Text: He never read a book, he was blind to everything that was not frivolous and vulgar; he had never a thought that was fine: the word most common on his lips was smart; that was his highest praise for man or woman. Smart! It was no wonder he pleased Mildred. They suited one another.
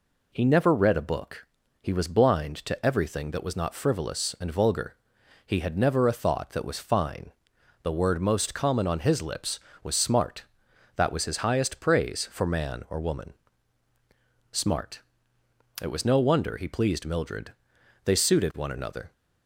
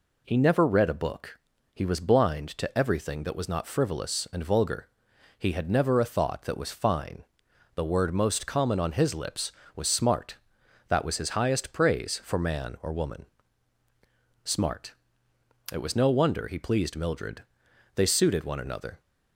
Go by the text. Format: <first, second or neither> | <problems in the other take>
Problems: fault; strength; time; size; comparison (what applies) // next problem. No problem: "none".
neither | none